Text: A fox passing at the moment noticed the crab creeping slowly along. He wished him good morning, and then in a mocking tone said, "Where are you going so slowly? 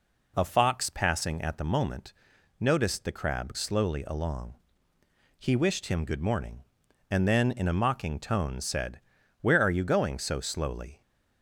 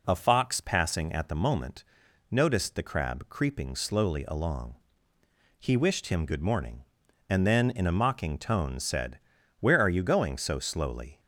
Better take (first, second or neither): second